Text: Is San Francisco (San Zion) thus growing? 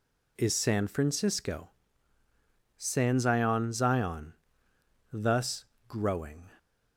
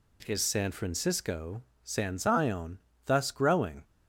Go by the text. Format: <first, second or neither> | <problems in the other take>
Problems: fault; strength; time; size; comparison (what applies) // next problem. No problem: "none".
second | says "Zion" twice; at 3.7 s // pauses between "thus" and "growing"; slight; at 5.6 s; 0.24 s long